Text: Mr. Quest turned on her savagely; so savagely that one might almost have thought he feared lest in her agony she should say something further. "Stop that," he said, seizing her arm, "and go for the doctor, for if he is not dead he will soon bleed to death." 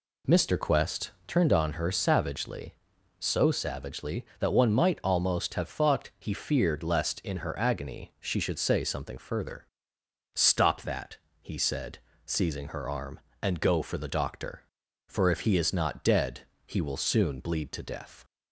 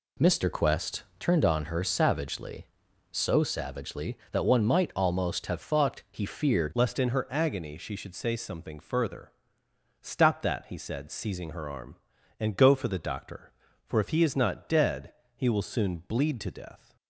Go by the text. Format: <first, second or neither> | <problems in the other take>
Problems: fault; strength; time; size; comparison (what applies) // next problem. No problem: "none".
first | pauses between "Quest" and "turned"; slight; at 1.0 s; 0.16 s long; slight in the first // changes voice at "lest"; from 6.7 s on; 10.2 s long // pauses between "dead" and "he"; slight; at 15.1 s; 0.22 s long; slight in the first